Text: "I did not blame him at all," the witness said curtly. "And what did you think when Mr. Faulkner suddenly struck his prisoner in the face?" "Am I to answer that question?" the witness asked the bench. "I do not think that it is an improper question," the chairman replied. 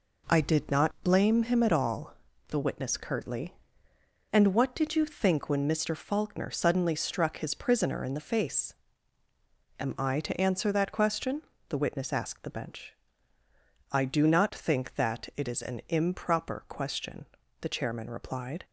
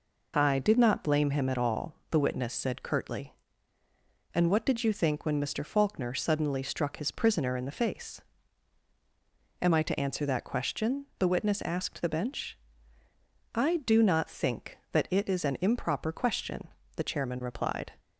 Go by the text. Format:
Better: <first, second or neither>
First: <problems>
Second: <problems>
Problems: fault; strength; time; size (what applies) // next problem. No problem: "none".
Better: second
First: skips "said"; at 2.9 s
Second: none